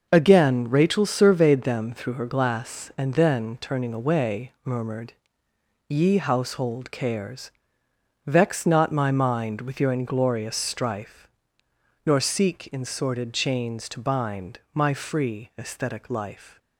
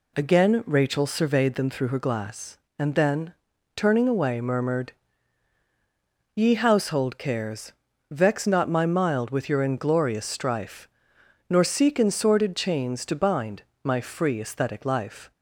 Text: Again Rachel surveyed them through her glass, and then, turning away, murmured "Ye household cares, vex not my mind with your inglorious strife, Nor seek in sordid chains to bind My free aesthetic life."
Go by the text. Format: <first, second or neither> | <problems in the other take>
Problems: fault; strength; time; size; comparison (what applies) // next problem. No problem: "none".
first | pauses between "murmured" and "Ye"; strong; at 4.9 s; 1.4 s long; noticeable in the first // says "mild" for "mind"; at 8.8 s // pauses between "bind" and "My"; slight; at 13.6 s; 0.20 s long